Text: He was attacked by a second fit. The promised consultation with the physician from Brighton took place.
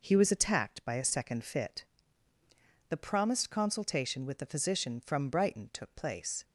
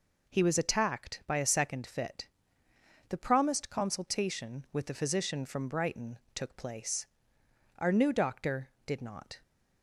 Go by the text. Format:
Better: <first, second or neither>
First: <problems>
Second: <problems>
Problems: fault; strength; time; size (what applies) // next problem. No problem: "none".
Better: first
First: none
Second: pauses between "Brighton" and "took"; slight; at 6.1 s; 0.16 s long // goes on to say "Our new doctor did not"; from 7.7 s on; 1.6 s long